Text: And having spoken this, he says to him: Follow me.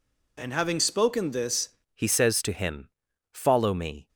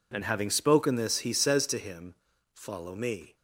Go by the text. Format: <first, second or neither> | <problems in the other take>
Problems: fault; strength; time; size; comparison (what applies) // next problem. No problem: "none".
second | changes voice at "he"; from 1.9 s on; 2.1 s long